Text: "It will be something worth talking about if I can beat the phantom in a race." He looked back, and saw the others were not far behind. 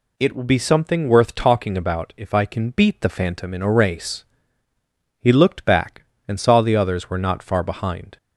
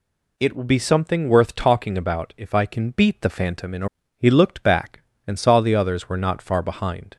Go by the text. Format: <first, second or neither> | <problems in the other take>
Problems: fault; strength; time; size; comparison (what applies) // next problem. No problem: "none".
first | skips "race"; at 4.0 s